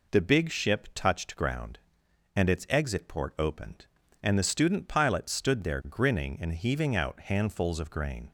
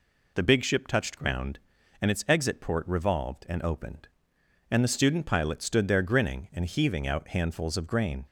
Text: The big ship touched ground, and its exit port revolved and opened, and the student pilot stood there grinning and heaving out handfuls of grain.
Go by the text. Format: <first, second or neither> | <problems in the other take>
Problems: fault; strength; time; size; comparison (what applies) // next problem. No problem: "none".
second | skips "revolved and"; at 3.3 s